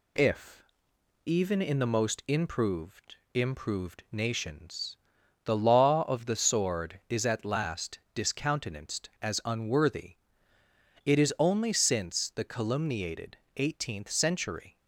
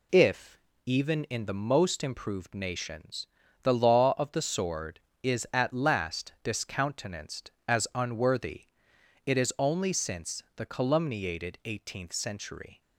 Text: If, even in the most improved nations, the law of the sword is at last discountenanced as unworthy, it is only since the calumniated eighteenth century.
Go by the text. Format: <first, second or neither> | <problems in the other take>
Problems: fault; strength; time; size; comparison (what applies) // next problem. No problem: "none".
second | says "improved" twice; at 3.3 s // pauses between "last" and "discountenanced"; slight; at 7.9 s; 0.16 s long // pauses between "calumniated" and "eighteenth"; slight; at 13.3 s; 0.20 s long